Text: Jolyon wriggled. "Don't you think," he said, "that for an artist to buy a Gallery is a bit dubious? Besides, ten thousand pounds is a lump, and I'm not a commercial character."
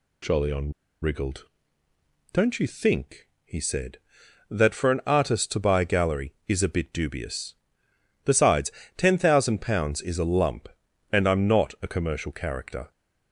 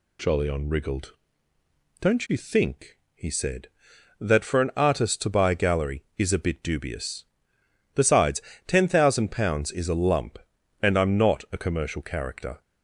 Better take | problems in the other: second | pauses between "Jolyon" and "wriggled"; slight; at 0.7 s; 0.30 s long

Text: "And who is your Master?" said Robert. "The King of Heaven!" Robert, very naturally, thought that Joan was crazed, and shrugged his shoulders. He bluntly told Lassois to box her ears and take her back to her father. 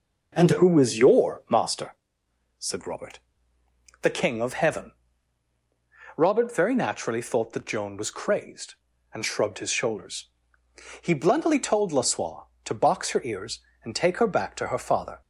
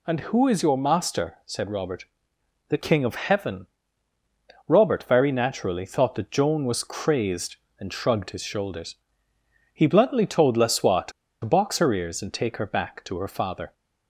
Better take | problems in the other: first | pauses between "to" and "box"; slight; at 11.1 s; 0.33 s long

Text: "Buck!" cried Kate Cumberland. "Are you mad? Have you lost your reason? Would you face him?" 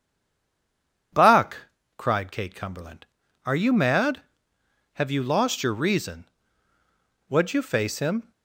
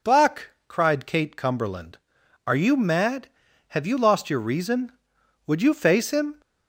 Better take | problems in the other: second | stays silent before the first word; until 1.1 s; 1.1 s long

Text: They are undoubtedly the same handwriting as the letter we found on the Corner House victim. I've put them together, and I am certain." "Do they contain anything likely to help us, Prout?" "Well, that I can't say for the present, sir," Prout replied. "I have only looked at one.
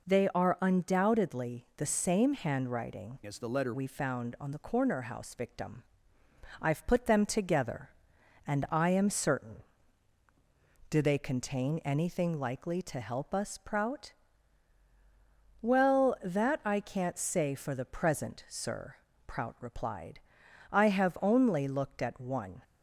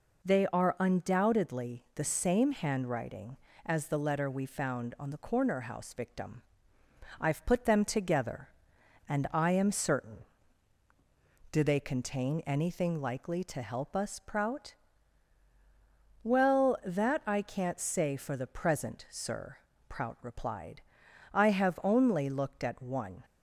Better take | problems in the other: second | changes voice from "as" to "letter"; from 3.2 to 3.7 s; 0.5 s long

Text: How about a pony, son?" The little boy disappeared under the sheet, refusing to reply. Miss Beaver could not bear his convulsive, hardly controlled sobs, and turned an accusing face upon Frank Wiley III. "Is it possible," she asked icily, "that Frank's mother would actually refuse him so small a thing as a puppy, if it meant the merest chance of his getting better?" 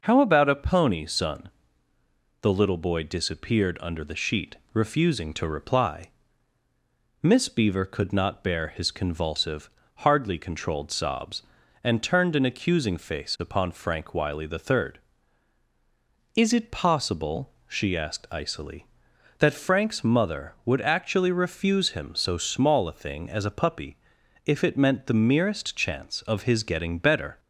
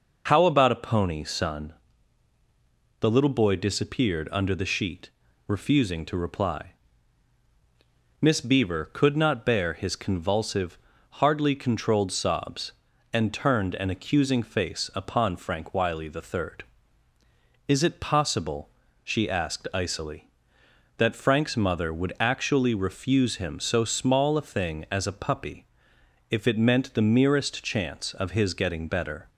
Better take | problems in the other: neither | none

